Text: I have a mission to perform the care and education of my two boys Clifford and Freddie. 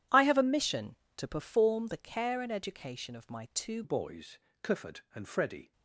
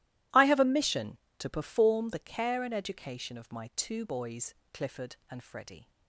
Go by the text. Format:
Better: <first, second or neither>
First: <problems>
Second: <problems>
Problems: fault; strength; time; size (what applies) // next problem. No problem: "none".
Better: second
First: changes voice at "boys"; from 3.8 s on; 1.9 s long // pauses between "boys" and "Clifford"; slight; at 4.3 s; 0.24 s long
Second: pauses between "boys" and "Clifford"; slight; at 4.5 s; 0.18 s long